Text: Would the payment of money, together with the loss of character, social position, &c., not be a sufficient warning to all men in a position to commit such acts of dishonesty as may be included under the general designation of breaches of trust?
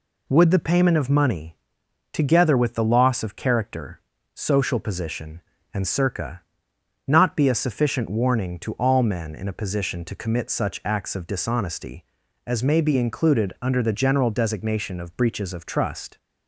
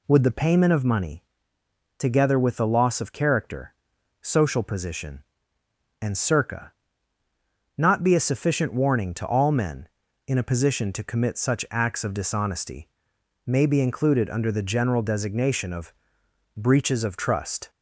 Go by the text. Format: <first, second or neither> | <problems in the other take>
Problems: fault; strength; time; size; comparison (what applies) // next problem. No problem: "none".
first | skips "as"; at 13.1 s // pauses between "of" and "breaches"; noticeable; at 15.9 s; 0.64 s long